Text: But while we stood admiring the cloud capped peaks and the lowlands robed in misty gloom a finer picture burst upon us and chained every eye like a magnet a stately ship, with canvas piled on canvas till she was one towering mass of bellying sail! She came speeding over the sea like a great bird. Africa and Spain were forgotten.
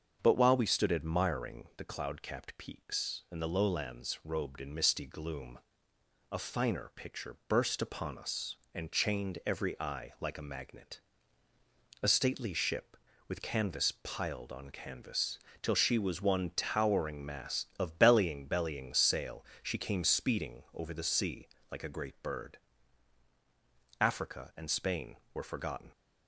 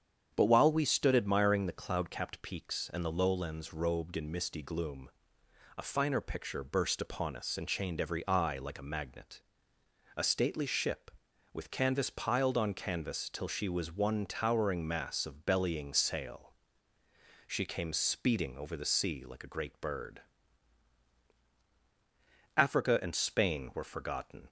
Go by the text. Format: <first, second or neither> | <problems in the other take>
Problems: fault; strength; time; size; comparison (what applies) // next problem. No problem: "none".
second | starts louder than the rest; until 1.2 s; 7 dB; strong in the second // pauses between "gloom" and "a"; noticeable; at 5.5 s; 0.72 s long; noticeable in the second // pauses between "magnet" and "a"; at 10.9 s; 1.0 s long; noticeable in the second // pauses between "canvas" and "till"; slight; at 15.3 s; 0.24 s long // says "bellying" twice; at 18.4 s // pauses between "sea" and "like"; slight; at 21.4 s; 0.26 s long